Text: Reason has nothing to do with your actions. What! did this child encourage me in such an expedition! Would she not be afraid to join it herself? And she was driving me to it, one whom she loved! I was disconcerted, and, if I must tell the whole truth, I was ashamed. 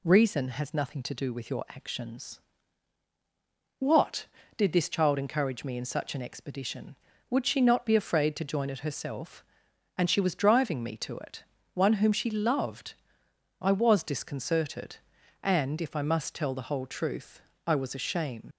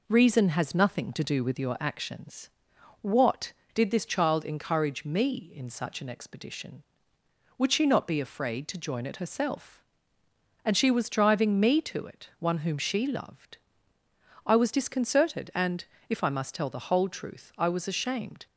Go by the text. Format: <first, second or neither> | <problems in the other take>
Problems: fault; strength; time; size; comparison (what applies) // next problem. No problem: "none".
second | leaves "ashamed" unfinished; at 18.5 s; 90 ms